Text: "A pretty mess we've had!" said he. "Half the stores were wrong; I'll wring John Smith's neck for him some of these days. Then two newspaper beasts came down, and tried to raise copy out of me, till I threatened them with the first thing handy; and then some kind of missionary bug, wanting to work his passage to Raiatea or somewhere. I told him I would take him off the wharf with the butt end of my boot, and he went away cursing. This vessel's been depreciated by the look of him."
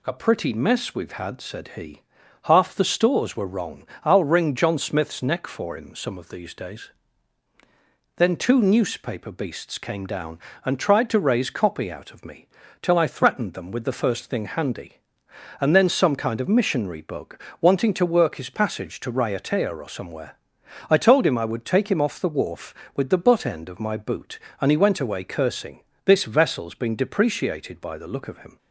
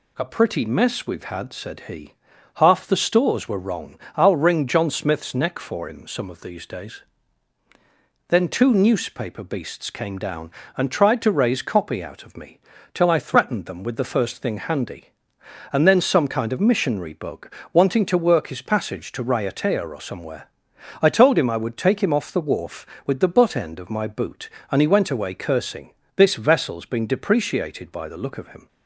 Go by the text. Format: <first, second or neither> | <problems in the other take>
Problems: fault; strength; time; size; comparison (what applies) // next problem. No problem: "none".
neither | none